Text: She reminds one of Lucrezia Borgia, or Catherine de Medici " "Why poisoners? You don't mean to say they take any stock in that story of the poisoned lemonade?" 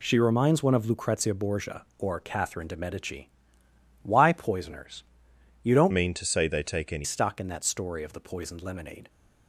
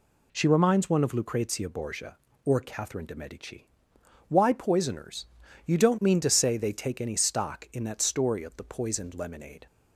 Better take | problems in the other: second | changes voice from "mean" to "any"; from 5.9 to 7.0 s; 1.1 s long

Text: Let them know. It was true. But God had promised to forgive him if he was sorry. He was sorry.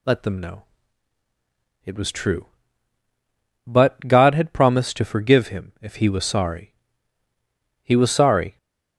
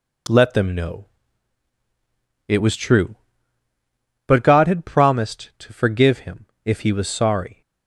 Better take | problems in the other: first | pauses between "him" and "if"; slight; at 6.4 s; 0.16 s long // stops before "He was sorry"; at 7.6 s

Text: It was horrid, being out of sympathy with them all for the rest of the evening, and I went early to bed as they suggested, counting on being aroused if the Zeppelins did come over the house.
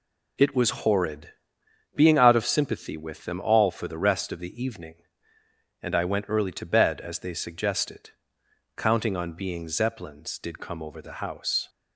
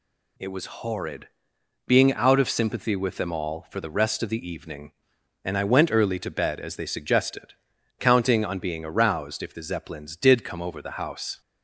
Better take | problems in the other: second | skips "aroused if the"; at 9.6 s

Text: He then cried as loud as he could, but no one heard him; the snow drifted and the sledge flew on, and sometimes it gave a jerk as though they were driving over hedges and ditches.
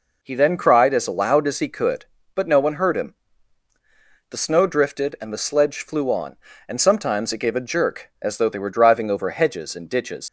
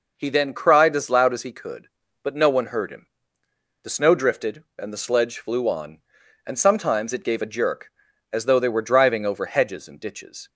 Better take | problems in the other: second | leaves "ditches" unfinished; at 10.2 s; 90 ms

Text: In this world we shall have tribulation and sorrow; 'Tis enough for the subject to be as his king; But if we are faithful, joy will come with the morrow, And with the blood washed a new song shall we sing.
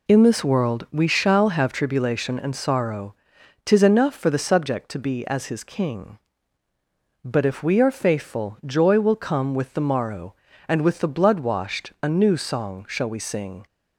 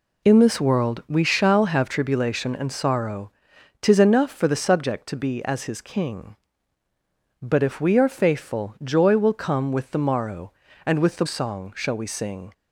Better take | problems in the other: first | skips "blood washed a new"; at 11.2 s

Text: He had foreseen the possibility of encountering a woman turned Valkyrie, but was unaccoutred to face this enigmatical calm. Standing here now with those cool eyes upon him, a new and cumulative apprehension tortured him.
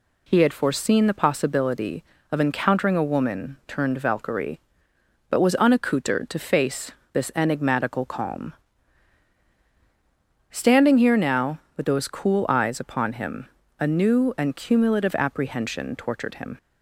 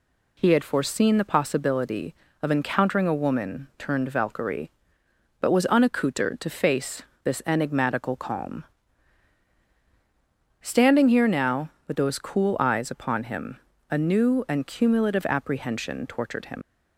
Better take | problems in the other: first | pauses between "face" and "this"; slight; at 7.0 s; 0.22 s long; slight in the first // leaves "him" unfinished; at 16.6 s; 65 ms

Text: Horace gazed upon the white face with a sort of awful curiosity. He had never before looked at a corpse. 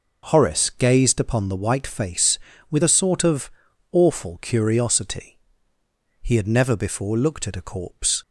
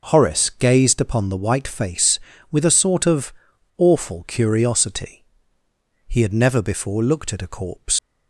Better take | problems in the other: first | pauses between "of" and "awful"; at 3.3 s; 0.43 s long; also in the first // leaves "corpse" unfinished; at 7.9 s; 85 ms

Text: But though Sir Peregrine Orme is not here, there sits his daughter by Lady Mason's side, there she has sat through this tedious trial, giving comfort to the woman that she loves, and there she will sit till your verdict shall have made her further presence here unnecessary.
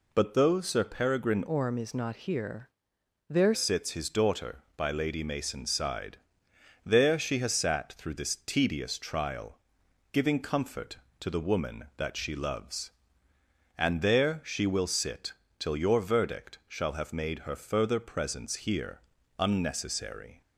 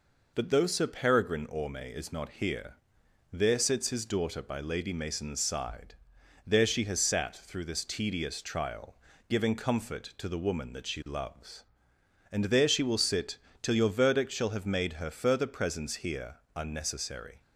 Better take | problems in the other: second | changes voice from "Orme" to "there"; from 1.4 to 3.5 s; 2.1 s long // pauses between "sit" and "till"; slight; at 15.3 s; 0.26 s long; slight in the second // pauses between "here" and "unnecessary"; slight; at 19.0 s; 0.36 s long; slight in the second

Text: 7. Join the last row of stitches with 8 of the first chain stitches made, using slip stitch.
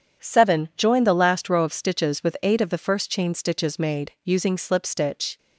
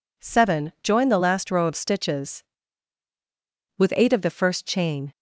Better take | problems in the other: first | stops before "stitches made using slip stitch"; at 5.1 s

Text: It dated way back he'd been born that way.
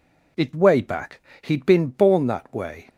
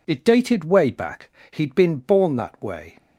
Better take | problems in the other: second | skips "dated"; at 0.5 s // pauses between "back" and "he'd"; slight; at 1.2 s; 0.20 s long; slight in the second

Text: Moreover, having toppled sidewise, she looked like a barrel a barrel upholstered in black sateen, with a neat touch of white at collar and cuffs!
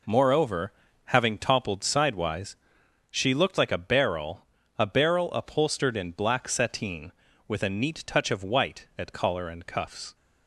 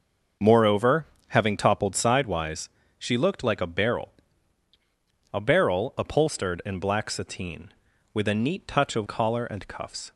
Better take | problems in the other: first | pauses between "barrel" and "a"; at 4.1 s; 1.2 s long; slight in the first // skips "white at"; at 9.0 s

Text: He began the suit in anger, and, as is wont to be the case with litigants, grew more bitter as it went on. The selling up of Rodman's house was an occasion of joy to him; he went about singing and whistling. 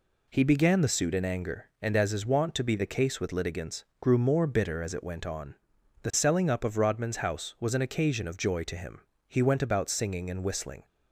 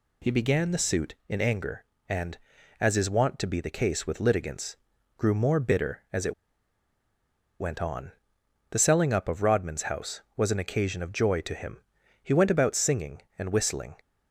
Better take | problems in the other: first | pauses between "it" and "went"; strong; at 6.3 s; 1.2 s long

